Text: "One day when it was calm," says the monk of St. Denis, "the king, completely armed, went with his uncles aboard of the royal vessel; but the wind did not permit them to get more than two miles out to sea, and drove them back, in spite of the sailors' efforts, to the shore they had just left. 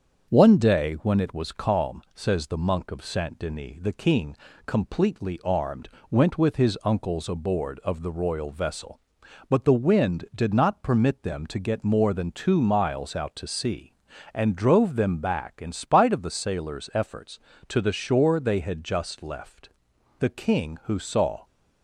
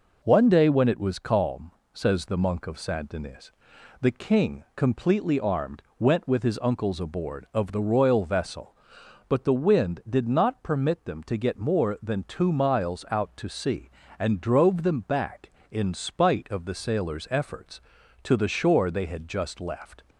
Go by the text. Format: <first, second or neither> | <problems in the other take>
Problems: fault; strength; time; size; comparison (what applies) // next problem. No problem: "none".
second | starts louder than the rest; until 1.3 s; 7 dB // goes on to say "The king who saw"; noticeable; from 20.1 s on; 1.2 s long